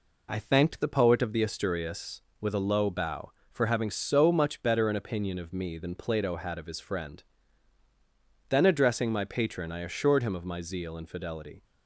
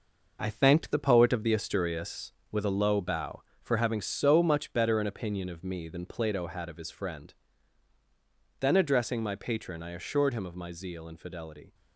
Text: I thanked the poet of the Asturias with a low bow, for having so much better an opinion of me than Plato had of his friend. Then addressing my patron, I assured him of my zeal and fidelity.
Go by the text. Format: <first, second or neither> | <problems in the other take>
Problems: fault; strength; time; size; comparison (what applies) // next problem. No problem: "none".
first | gets quieter; strong; throughout; 7.5 dB